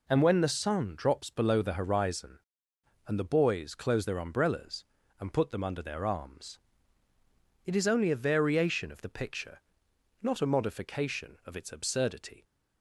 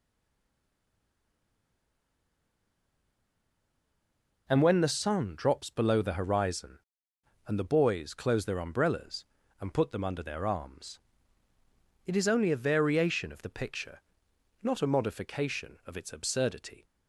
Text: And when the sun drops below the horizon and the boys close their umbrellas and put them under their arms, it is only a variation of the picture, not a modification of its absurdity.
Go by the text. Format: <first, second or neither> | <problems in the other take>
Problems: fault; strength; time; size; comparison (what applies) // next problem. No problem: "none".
first | stays silent before the first word; strong; until 4.4 s; 4.4 s long